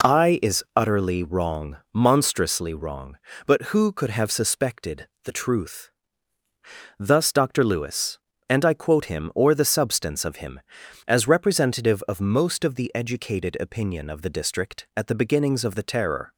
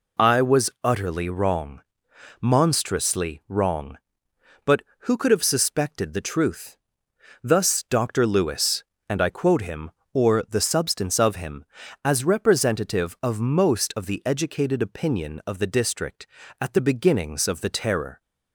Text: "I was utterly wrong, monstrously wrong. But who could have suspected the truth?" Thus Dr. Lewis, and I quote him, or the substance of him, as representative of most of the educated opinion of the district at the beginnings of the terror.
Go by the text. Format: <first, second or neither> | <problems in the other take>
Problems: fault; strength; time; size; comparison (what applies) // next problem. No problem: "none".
second | says "is" for "was"; at 0.4 s // pauses between "suspected" and "the"; slight; at 5.0 s; 0.18 s long